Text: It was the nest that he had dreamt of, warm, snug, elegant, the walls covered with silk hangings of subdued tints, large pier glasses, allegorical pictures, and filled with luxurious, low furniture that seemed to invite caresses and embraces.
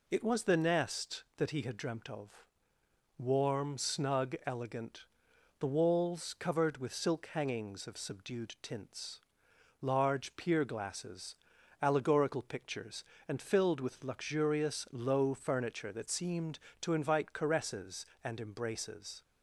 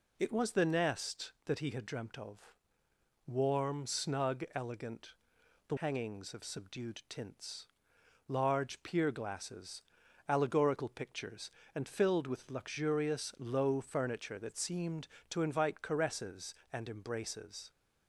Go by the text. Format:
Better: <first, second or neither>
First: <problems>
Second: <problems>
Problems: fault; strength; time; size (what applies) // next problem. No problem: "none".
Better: first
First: none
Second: skips "walls covered with silk"; at 5.7 s